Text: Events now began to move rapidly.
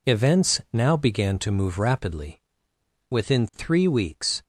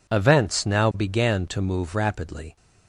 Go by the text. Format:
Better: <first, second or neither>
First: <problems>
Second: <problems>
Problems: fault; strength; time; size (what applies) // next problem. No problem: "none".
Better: second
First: goes on to say "Within three weeks"; from 3.0 s on; 1.3 s long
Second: none